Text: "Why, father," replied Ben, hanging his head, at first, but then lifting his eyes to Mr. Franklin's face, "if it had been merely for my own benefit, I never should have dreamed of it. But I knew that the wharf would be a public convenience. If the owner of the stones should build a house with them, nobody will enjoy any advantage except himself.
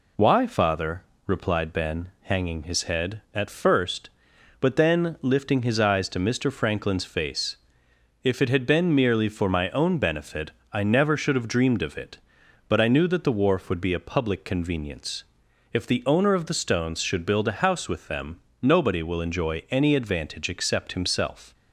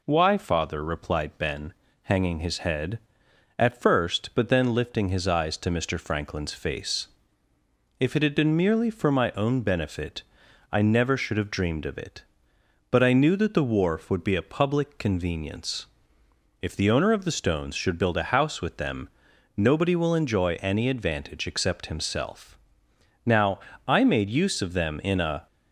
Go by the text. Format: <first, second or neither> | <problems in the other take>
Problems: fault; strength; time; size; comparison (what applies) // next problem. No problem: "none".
first | goes on to say "Now I made use of them in a"; strong; from 23.2 s on; 2.2 s long